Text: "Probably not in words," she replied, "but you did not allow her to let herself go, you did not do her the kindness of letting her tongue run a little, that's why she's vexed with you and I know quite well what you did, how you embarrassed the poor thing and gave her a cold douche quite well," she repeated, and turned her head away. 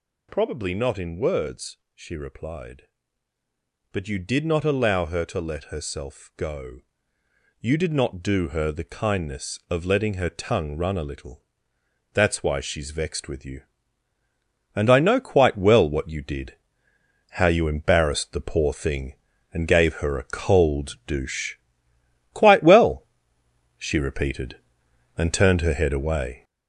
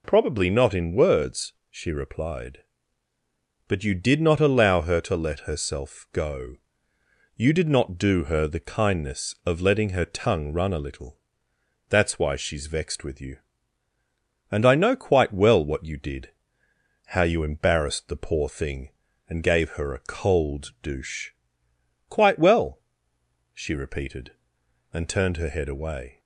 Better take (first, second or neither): second